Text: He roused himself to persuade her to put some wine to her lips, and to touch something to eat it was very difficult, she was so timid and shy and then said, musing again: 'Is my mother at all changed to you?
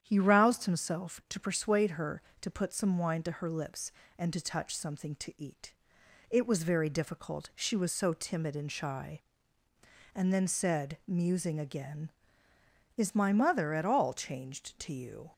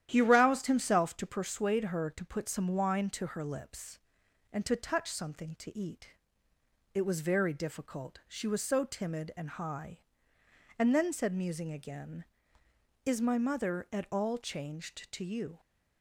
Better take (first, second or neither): first